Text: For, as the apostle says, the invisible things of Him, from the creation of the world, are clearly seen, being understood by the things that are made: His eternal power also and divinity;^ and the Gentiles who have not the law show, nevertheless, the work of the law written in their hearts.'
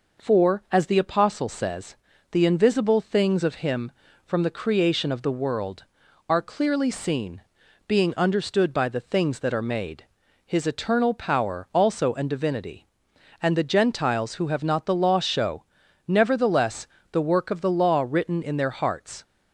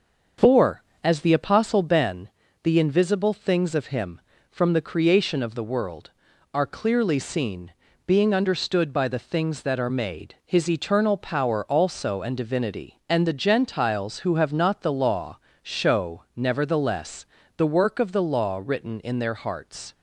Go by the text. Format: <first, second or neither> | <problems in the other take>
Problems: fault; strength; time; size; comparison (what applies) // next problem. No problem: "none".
first | starts louder than the rest; until 1.6 s; 6.5 dB // says "ben" for "says"; at 1.8 s // pauses between "law" and "show"; slight; at 15.3 s; 0.26 s long